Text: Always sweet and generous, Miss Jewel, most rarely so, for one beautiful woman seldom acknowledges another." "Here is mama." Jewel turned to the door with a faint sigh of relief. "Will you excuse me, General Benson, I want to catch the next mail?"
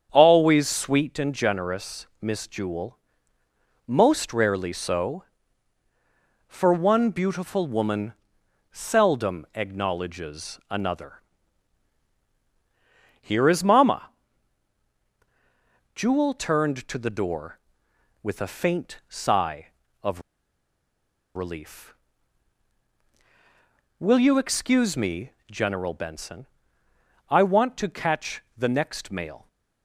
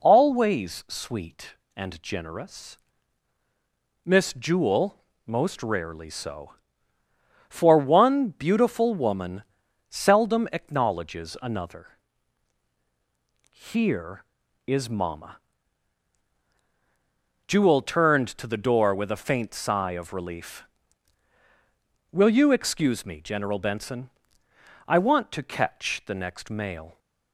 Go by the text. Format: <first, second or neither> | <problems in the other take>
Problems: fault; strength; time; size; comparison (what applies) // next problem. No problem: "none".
second | starts louder than the rest; strong; until 1.1 s; 7.5 dB // pauses between "woman" and "seldom"; noticeable; at 8.1 s; 0.58 s long; noticeable in the second // pauses between "of" and "relief"; at 20.2 s; 1.1 s long // pauses between "catch" and "the"; slight; at 28.4 s; 0.16 s long